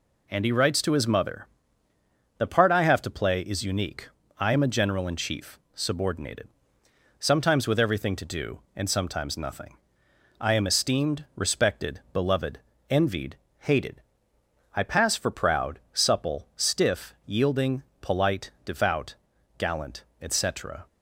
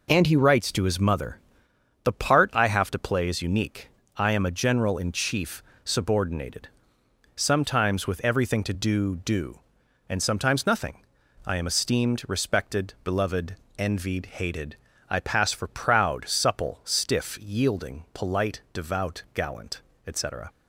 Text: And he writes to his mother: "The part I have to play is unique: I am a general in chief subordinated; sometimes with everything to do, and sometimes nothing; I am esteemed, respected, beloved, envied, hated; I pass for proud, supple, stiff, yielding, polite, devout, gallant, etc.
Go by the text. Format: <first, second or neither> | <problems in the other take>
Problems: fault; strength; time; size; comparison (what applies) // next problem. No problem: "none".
first | pauses between "chief" and "subordinated"; slight; at 5.6 s; 0.24 s long; slight in the first // says "do" twice; at 9.1 s